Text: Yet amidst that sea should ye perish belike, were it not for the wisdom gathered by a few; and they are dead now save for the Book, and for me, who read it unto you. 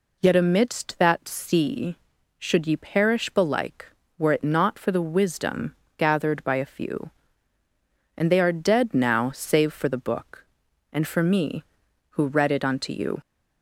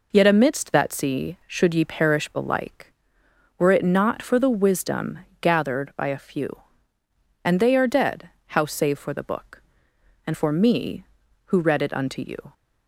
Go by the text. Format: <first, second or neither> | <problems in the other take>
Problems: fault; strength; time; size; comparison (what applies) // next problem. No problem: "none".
first | pauses between "wisdom" and "gathered"; slight; at 5.1 s; 0.22 s long; slight in the first // says "how" for "now"; at 8.4 s